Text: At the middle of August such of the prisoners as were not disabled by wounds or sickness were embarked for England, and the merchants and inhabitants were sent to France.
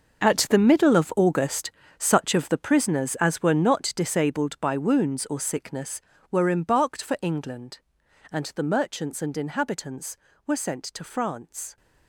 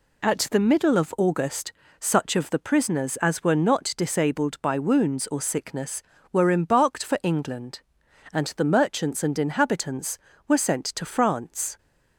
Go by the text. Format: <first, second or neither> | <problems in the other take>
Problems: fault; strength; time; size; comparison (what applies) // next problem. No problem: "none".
second | gets quieter; strong; throughout; 14 dB // pauses between "August" and "such"; slight; at 1.7 s; 0.26 s long; slight in the second